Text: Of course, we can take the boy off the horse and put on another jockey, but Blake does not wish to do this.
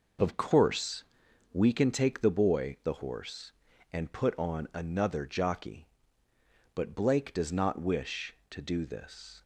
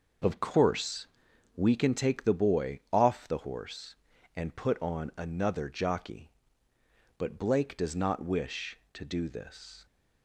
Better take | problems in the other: second | skips "off"; at 2.8 s

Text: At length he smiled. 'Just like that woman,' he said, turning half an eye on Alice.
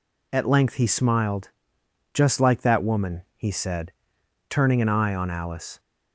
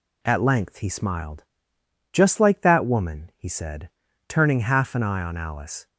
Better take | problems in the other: second | skips "half"; at 4.8 s

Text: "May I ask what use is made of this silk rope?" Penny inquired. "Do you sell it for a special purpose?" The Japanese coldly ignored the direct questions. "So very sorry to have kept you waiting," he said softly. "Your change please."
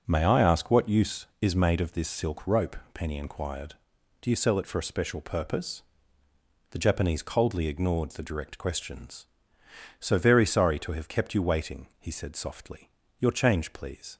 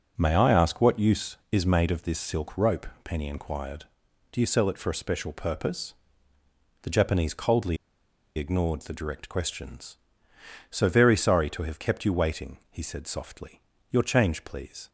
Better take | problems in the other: first | pauses between "coldly" and "ignored"; noticeable; at 7.7 s; 0.61 s long

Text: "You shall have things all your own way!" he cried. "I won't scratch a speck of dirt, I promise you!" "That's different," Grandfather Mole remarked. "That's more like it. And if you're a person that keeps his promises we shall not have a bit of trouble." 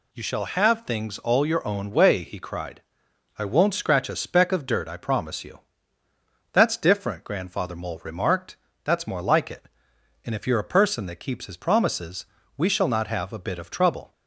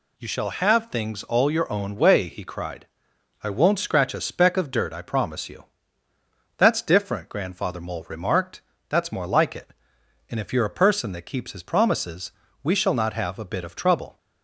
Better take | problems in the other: neither | pauses between "promises" and "we"; slight; the same in both

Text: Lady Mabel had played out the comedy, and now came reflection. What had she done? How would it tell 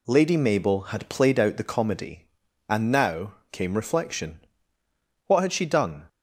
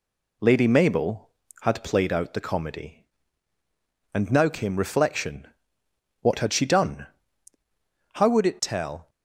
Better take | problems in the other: second | pauses between "now" and "came"; slight; at 3.3 s; 0.18 s long // stops before "How would it tell"; at 6.0 s

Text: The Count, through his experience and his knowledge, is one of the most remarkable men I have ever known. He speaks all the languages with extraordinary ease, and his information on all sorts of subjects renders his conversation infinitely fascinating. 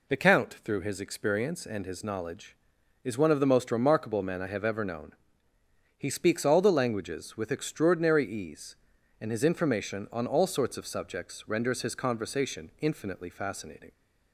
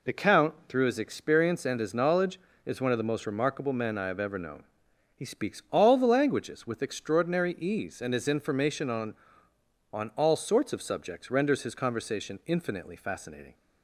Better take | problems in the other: first | says "on" twice; at 9.9 s

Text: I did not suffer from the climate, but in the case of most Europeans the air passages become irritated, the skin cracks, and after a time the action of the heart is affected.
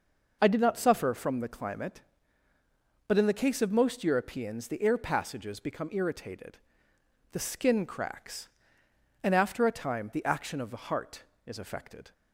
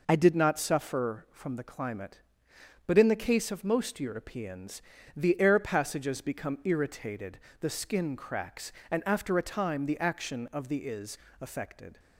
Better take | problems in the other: first | pauses between "Europeans" and "the"; slight; at 4.8 s; 0.34 s long // skips "heart"; at 10.8 s // pauses between "is" and "affected"; slight; at 11.1 s; 0.22 s long

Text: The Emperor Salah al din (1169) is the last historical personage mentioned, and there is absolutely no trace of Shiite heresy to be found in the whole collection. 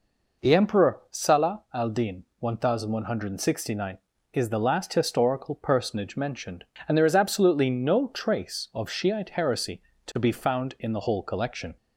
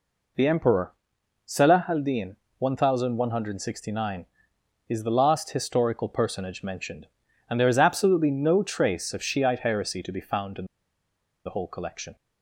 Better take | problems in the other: first | pauses between "Emperor" and "Salah"; noticeable; at 0.9 s; 0.54 s long // pauses between "in" and "the"; noticeable; at 10.6 s; 0.80 s long

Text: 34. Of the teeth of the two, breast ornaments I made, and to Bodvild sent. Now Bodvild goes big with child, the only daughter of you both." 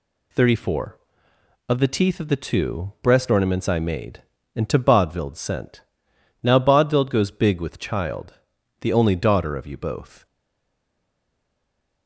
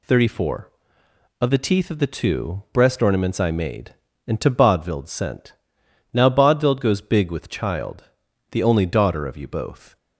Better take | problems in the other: second | stays silent after the last word; noticeable; from 10.2 s on; 1.8 s long

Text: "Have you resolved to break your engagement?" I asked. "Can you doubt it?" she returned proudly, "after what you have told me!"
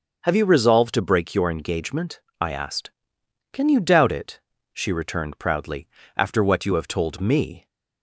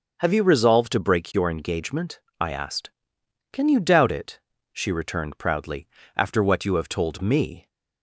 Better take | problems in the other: neither | starts louder than the rest; the same in both

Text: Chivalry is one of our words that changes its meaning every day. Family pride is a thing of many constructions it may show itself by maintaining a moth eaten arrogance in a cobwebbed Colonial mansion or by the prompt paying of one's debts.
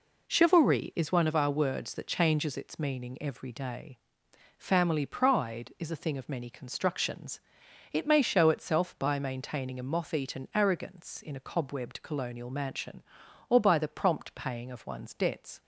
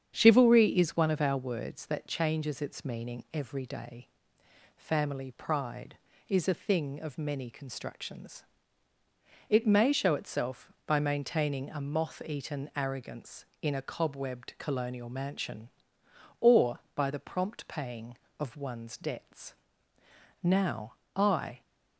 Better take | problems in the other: first | starts louder than the rest; strong; until 1.1 s; 8 dB // pauses between "constructions" and "it"; at 8.4 s; 1.0 s long; noticeable in the first // goes on to say "Now I"; noticeable; from 20.4 s on; 1.1 s long

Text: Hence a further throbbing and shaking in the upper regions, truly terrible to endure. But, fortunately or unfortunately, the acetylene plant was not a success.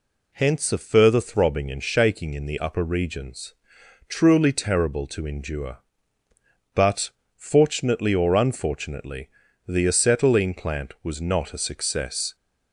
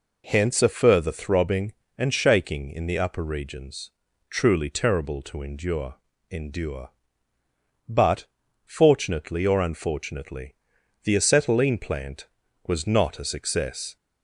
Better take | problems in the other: first | says "endure" twice; at 6.3 s

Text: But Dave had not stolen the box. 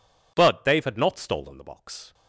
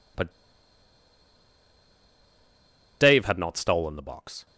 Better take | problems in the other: first | pauses between "But" and "Dave"; strong; at 0.3 s; 2.6 s long

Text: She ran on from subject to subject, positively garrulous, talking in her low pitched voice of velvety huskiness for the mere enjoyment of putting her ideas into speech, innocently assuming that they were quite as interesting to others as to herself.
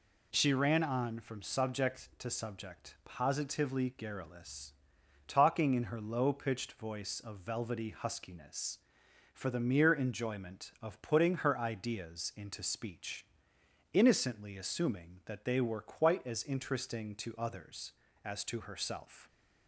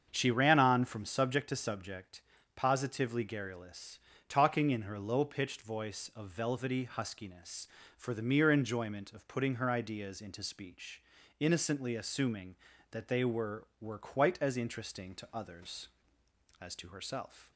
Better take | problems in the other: first | starts louder than the rest; strong; until 1.1 s; 7 dB // says "were" twice; at 13.7 s

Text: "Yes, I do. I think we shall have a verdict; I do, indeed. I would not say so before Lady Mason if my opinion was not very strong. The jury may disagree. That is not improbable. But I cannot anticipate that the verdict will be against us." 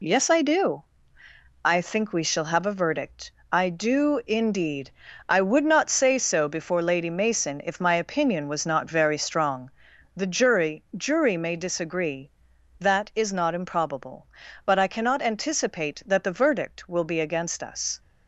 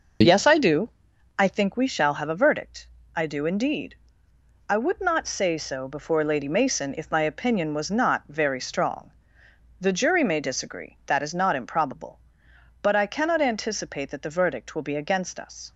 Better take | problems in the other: second | says "jury" twice; at 10.9 s

